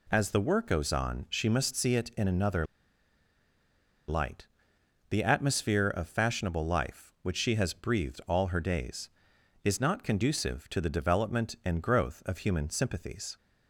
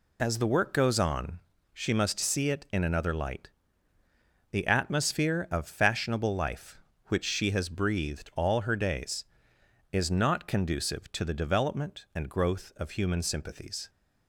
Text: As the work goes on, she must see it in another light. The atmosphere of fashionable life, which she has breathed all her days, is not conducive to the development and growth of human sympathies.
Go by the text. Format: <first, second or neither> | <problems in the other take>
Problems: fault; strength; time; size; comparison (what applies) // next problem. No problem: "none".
second | pauses between "another" and "light"; strong; at 2.6 s; 1.4 s long